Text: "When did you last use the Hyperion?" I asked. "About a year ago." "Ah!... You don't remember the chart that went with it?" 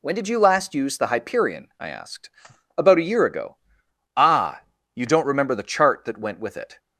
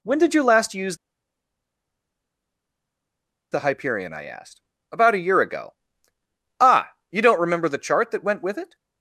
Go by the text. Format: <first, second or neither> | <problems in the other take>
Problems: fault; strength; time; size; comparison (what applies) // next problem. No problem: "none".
first | pauses between "use" and "the"; strong; at 0.9 s; 2.5 s long